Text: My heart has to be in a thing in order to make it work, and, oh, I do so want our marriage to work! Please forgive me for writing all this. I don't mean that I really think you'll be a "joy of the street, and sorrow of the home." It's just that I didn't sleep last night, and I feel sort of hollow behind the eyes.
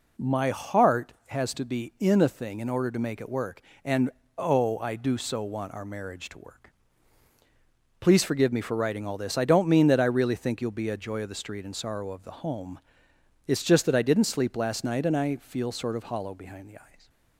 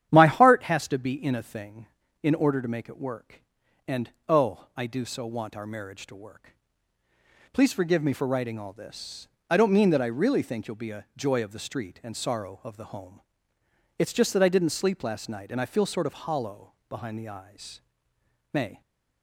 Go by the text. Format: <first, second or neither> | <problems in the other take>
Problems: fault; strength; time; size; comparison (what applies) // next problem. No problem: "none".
first | starts louder than the rest; strong; until 1.1 s; 10 dB // pauses between "hollow" and "behind"; slight; at 16.7 s; 0.16 s long // goes on to say "May"; slight; from 18.5 s on; 0.30 s long